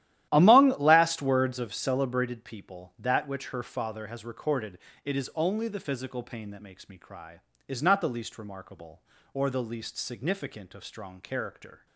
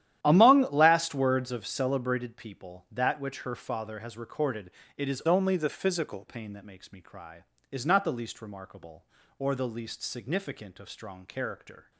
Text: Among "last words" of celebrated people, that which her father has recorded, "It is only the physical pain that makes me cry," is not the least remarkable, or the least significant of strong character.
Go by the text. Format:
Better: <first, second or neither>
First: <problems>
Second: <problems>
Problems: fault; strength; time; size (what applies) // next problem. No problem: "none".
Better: first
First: starts louder than the rest; strong; until 1.3 s; 13 dB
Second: starts louder than the rest; strong; until 1.2 s; 11.5 dB // changes voice from "only" to "physical"; from 5.2 to 6.2 s; 1.0 s long